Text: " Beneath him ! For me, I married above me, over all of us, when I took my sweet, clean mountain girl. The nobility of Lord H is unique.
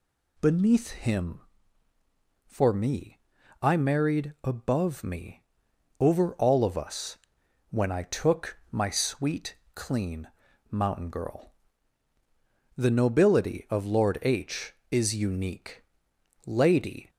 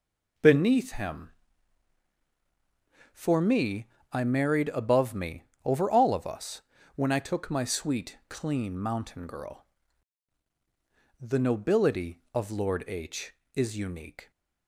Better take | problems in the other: second | pauses between "clean" and "mountain"; at 10.2 s; 0.42 s long // goes on to say "Lady"; noticeable; from 16.4 s on; 0.64 s long

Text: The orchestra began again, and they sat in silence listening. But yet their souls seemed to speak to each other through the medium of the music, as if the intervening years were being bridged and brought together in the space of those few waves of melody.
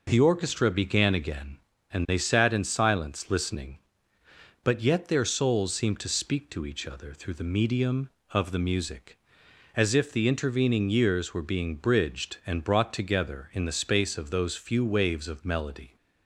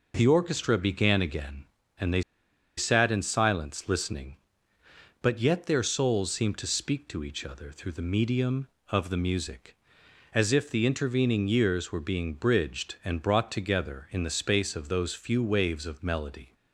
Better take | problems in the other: first | pauses between "they" and "sat"; noticeable; at 2.2 s; 0.56 s long

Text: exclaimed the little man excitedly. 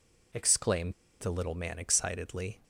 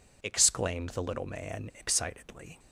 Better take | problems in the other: second | pauses between "exclaimed" and "the"; slight; at 0.9 s; 0.27 s long

